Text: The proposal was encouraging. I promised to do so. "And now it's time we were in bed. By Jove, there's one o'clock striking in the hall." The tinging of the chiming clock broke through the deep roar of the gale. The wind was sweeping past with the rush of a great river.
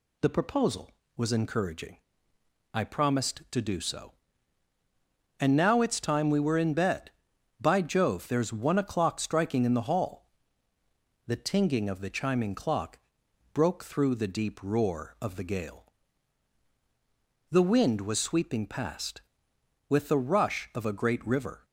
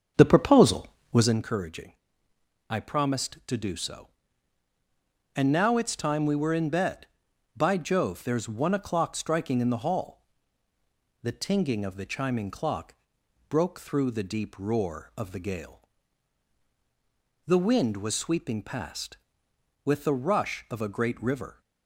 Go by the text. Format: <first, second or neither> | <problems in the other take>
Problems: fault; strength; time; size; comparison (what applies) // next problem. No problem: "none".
first | starts louder than the rest; strong; until 1.4 s; 7 dB // pauses between "clock" and "broke"; noticeable; at 12.9 s; 0.54 s long; noticeable in the first